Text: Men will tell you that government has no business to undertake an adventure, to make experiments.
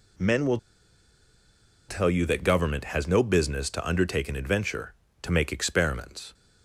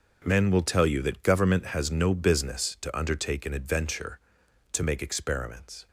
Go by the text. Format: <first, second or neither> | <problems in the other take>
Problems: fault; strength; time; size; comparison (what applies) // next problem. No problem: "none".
second | pauses between "will" and "tell"; strong; at 0.5 s; 1.3 s long